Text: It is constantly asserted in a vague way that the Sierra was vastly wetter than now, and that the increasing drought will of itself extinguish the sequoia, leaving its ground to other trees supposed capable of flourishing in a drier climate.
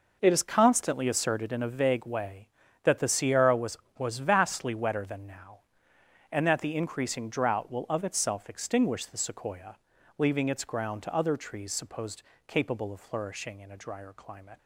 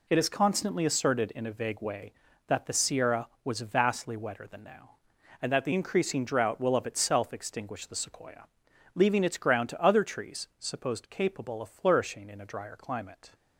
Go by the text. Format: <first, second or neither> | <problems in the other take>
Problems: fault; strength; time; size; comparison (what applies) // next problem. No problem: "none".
second | says "was" twice; at 3.9 s // pauses between "supposed" and "capable"; slight; at 12.2 s; 0.26 s long